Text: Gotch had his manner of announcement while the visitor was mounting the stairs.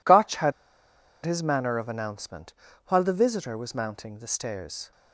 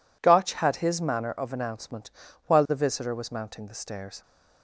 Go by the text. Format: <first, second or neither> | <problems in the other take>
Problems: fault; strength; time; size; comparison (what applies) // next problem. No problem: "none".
second | pauses between "had" and "his"; noticeable; at 0.5 s; 0.72 s long // pauses between "announcement" and "while"; slight; at 2.5 s; 0.34 s long; slight in the second